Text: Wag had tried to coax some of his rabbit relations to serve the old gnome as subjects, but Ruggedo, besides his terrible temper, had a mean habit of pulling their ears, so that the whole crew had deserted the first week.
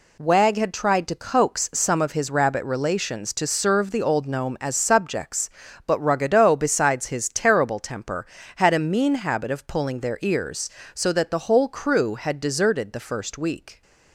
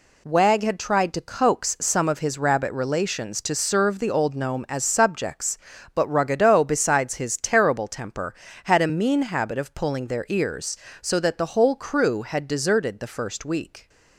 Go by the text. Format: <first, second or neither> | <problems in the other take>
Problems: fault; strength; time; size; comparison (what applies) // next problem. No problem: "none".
neither | none